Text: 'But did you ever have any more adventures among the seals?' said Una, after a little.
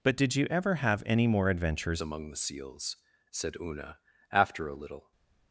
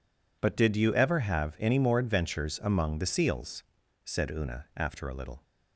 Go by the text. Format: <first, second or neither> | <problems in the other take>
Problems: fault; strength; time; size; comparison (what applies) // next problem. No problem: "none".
second | changes voice at "among"; from 2.0 s on; 3.1 s long // stays silent after the last word; slight; from 5.0 s on; 0.5 s long